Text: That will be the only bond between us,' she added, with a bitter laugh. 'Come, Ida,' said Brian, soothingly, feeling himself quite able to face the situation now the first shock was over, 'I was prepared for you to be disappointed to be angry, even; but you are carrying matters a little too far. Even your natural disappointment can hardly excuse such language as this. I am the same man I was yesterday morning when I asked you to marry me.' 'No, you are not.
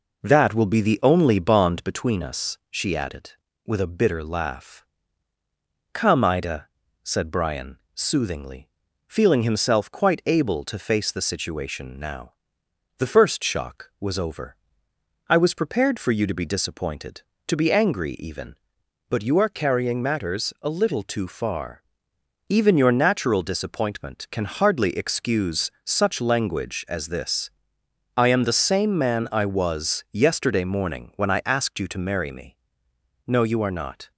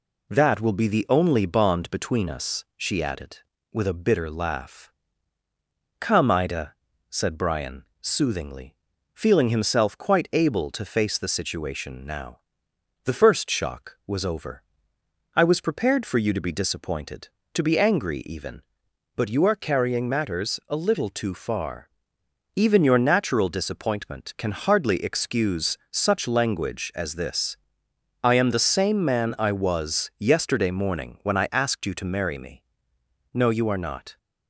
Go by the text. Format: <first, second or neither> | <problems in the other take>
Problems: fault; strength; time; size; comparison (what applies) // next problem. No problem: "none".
second | starts louder than the rest; noticeable; until 1.9 s; 4.5 dB // pauses between "now" and "the"; noticeable; at 12.3 s; 0.66 s long; noticeable in the second